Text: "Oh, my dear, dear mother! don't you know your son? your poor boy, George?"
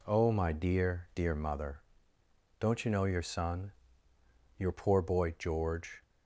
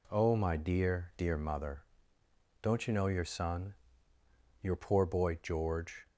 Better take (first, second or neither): neither